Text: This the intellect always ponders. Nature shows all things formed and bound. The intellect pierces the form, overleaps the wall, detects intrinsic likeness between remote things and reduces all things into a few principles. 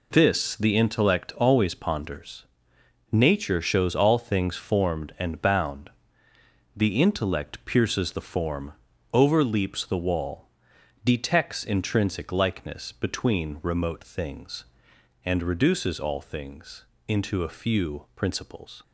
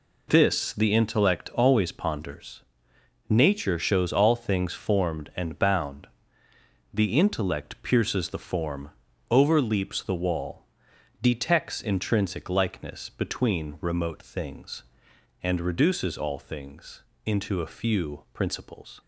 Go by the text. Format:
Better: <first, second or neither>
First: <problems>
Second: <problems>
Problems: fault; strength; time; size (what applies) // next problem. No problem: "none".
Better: neither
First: pauses between "things" and "into"; slight; at 16.8 s; 0.22 s long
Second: pauses between "things" and "into"; slight; at 17.0 s; 0.22 s long